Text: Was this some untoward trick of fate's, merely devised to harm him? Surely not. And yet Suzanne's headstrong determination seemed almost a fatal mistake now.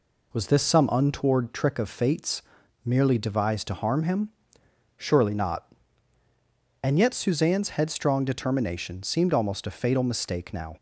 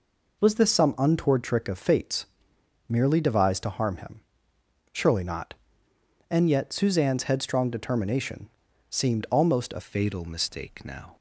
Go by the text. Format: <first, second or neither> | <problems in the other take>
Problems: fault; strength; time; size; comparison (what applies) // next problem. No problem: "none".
first | pauses between "determination" and "seemed"; at 8.4 s; 0.40 s long // changes voice at "fatal"; from 9.8 s on; 1.3 s long